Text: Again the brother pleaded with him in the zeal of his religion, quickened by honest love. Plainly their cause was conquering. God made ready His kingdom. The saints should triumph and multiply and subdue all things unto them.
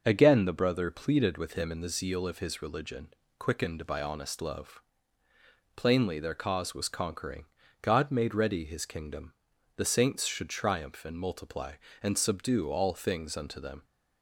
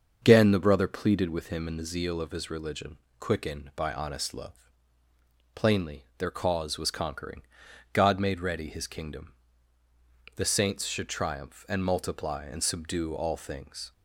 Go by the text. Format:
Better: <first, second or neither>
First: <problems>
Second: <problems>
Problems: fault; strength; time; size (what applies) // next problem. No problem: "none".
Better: first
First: none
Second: starts louder than the rest; until 1.2 s; 6.5 dB // stops before "unto them"; at 13.9 s